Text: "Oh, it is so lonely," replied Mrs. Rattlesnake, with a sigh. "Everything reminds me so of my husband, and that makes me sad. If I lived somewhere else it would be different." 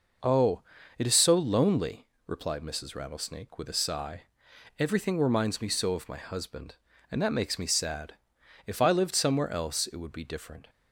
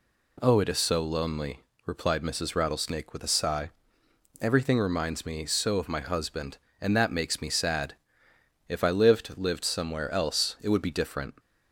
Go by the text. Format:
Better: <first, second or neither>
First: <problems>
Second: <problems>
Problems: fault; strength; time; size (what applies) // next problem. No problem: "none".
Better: first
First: none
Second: says "lived" twice; at 9.3 s